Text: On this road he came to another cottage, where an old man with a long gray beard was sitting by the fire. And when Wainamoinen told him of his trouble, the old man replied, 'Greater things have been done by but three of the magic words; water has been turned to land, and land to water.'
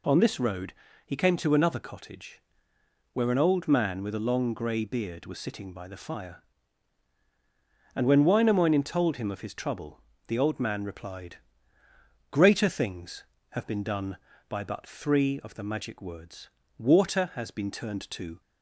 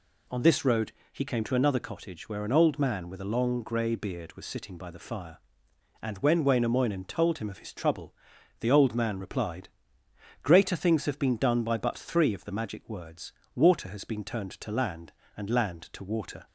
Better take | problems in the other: second | pauses between "road" and "he"; slight; at 0.7 s; 0.32 s long; slight in the second // stops before "land and land to water"; at 18.4 s

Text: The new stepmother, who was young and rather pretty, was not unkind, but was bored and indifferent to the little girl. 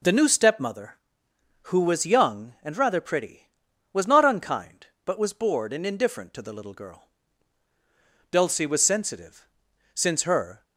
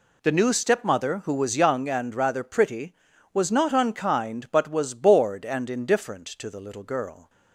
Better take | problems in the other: second | goes on to say "Dulcie was sensitive since her"; strong; from 8.2 s on; 2.3 s long

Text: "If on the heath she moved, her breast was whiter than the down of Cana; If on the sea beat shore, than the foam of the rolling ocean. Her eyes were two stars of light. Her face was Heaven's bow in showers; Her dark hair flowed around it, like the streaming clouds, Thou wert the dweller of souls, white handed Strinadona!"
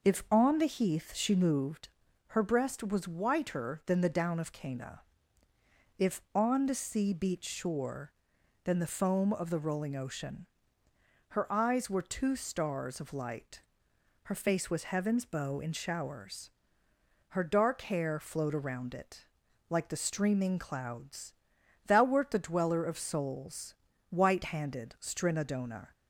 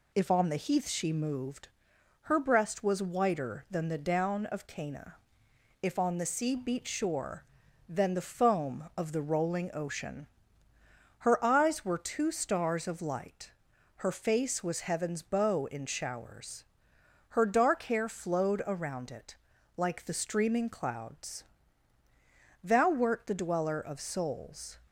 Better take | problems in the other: first | stops before "white handed Strinadona"; at 24.8 s

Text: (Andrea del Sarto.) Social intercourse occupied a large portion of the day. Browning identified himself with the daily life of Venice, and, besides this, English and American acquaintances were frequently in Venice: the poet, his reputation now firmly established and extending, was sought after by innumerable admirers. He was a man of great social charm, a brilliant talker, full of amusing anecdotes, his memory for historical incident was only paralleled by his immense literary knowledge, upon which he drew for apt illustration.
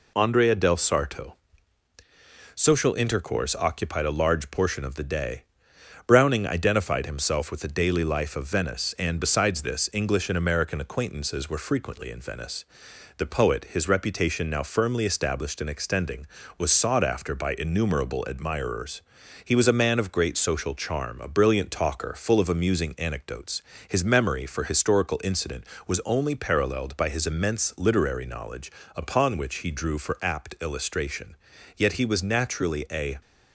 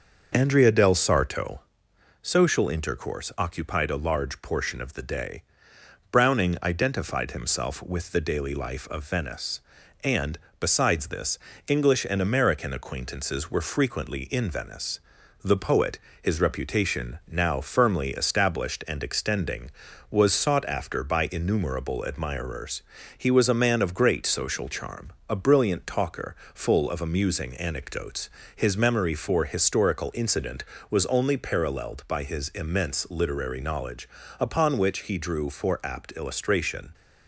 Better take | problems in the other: second | goes on to say "Yet he was naturally a"; from 31.7 s on; 1.4 s long

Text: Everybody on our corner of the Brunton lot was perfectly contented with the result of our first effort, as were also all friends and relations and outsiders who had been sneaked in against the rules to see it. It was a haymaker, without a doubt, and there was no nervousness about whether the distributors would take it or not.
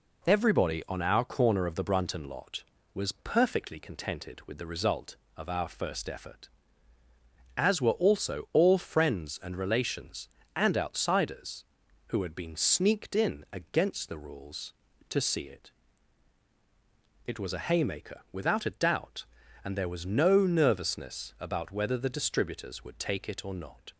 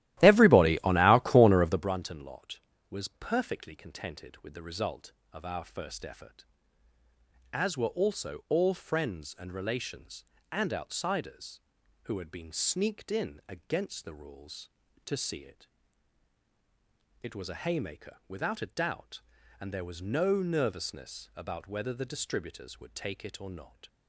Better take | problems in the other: first | starts louder than the rest; strong; until 1.9 s; 14.5 dB

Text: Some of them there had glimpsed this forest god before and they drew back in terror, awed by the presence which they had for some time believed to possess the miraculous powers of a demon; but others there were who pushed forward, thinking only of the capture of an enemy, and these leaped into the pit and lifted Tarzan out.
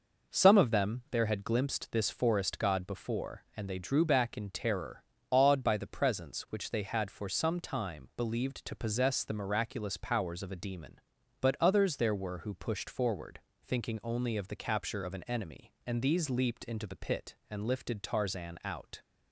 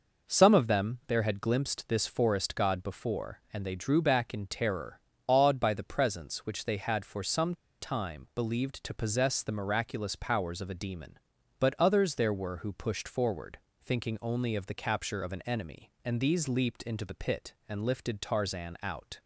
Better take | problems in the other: first | pauses between "some" and "time"; slight; at 7.5 s; 0.26 s long

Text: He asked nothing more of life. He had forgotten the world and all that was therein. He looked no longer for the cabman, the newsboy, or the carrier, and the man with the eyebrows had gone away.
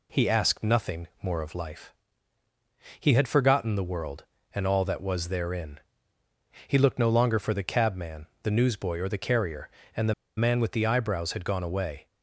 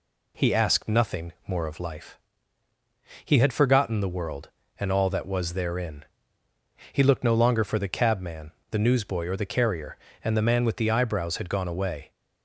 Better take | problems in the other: second | pauses between "nothing" and "more"; slight; at 1.0 s; 0.16 s long; slight in the second // pauses between "the" and "man"; slight; at 10.1 s; 0.24 s long

